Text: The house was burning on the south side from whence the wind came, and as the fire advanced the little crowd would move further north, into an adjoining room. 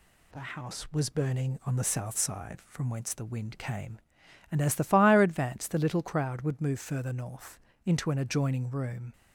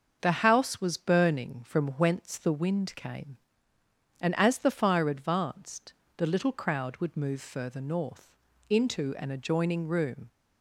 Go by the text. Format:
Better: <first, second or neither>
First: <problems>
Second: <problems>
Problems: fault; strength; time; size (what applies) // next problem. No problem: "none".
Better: first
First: none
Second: starts louder than the rest; until 1.2 s; 6.5 dB // skips "on the south side"; at 1.6 s // pauses between "advanced" and "the"; slight; at 5.9 s; 0.24 s long